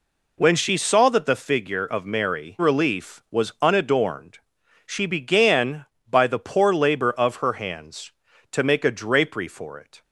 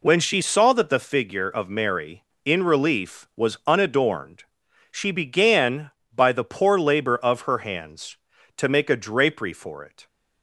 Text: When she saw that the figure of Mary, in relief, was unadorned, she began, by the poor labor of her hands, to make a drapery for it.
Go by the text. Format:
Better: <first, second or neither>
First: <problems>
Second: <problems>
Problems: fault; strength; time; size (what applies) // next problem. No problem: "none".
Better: second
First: skips "in"; at 2.5 s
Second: none